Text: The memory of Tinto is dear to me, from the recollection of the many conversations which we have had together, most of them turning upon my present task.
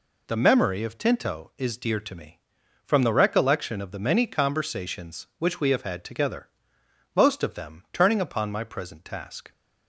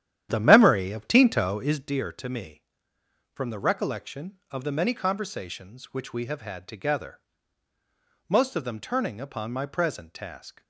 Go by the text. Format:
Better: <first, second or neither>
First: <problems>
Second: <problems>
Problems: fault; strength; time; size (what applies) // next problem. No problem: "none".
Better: first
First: none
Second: starts louder than the rest; strong; until 1.9 s; 10.5 dB